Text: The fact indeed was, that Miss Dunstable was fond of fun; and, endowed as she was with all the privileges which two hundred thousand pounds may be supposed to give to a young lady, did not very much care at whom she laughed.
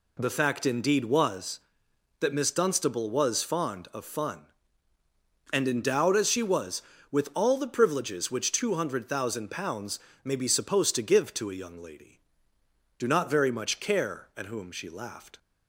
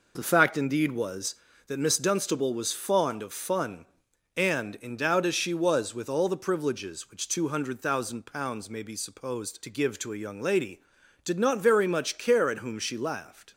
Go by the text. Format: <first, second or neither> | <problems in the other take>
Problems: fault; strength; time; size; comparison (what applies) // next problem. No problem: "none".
second | pauses between "pounds" and "may"; slight; at 9.9 s; 0.24 s long // says "do" for "did"; at 12.9 s